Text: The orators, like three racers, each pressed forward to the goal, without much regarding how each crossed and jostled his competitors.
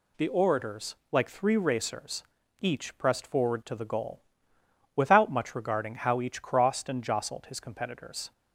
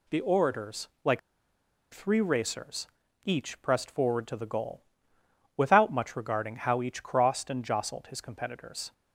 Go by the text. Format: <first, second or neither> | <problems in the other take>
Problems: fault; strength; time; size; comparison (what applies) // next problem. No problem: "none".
first | pauses between "like" and "three"; noticeable; at 1.1 s; 0.72 s long